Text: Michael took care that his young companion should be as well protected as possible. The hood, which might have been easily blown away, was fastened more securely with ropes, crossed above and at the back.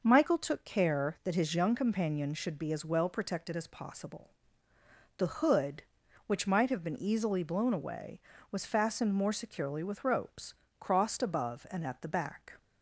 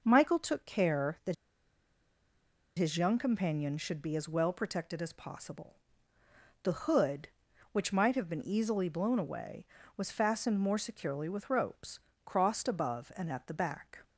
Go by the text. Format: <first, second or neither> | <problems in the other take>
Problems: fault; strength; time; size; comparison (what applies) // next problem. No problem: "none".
first | pauses between "that" and "his"; strong; at 1.3 s; 1.4 s long